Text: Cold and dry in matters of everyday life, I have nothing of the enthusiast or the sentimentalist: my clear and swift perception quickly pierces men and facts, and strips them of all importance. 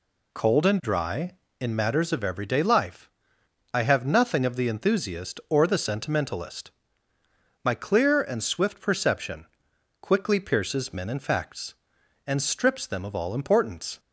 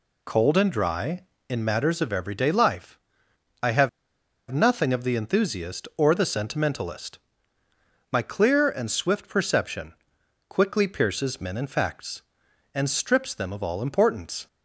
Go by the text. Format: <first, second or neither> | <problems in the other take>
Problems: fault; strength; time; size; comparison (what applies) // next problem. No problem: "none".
first | pauses between "have" and "nothing"; noticeable; at 3.8 s; 0.63 s long // pauses between "perception" and "quickly"; noticeable; at 9.9 s; 0.56 s long; noticeable in the first